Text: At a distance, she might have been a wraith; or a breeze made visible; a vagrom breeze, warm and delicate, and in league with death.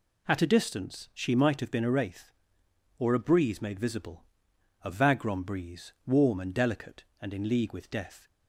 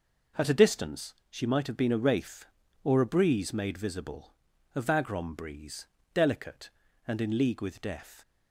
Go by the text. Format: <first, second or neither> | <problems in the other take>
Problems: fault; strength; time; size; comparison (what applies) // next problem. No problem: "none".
first | skips "warm and"; at 6.0 s